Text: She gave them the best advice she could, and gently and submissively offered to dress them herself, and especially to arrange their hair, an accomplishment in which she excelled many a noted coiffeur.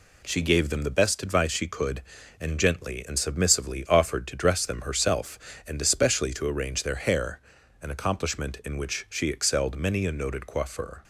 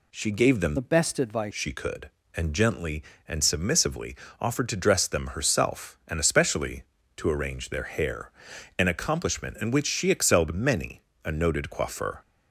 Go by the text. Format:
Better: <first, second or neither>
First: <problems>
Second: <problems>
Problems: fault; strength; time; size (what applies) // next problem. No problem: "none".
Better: first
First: none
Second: changes voice from "the" to "advice"; from 0.7 to 1.5 s; 0.8 s long // pauses between "submissively" and "offered"; slight; at 4.1 s; 0.24 s long // pauses between "many" and "a"; slight; at 11.0 s; 0.24 s long